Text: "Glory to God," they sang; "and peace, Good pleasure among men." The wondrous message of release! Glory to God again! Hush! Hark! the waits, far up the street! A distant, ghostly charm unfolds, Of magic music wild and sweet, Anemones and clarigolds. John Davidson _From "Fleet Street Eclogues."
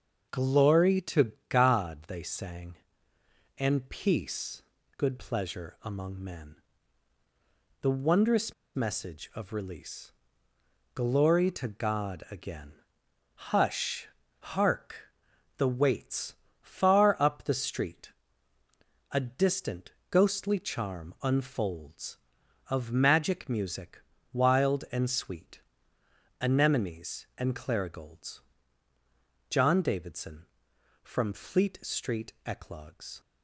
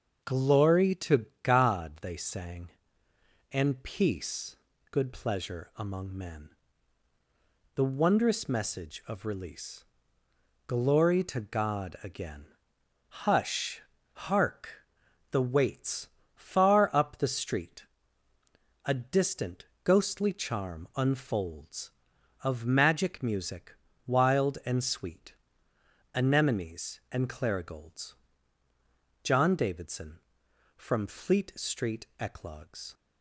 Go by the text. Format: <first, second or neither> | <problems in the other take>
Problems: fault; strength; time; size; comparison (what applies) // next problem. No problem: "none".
second | starts louder than the rest; until 1.3 s; 6 dB; also in the second // pauses between "to" and "God"; slight; at 1.3 s; 0.16 s long; slight in the second // pauses between "wondrous" and "message"; slight; at 8.5 s; 0.22 s long // pauses between "music" and "wild"; slight; at 23.9 s; 0.32 s long; slight in the second